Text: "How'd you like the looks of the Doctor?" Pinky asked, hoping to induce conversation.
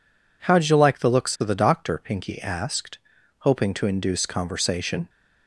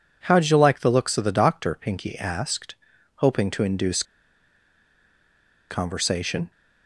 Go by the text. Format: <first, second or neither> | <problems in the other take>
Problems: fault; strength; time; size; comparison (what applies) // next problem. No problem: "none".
first | pauses between "induce" and "conversation"; strong; at 4.0 s; 1.6 s long